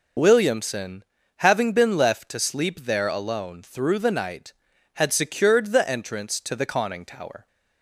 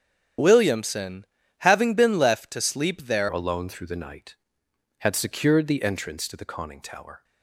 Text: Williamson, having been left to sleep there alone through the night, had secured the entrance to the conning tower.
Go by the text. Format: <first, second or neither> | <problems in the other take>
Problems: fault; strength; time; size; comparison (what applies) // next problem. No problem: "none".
first | starts louder than the rest; strong; until 1.7 s; 9 dB // changes voice at "alone"; from 3.2 s on; 4.0 s long